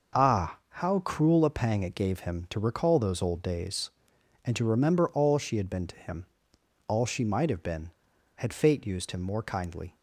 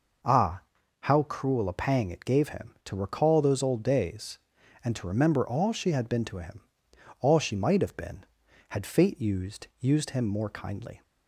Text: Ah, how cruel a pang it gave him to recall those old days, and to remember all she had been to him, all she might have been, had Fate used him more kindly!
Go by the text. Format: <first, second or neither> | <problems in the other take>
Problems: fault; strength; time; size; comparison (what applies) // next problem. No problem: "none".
first | says "used" twice; at 9.7 s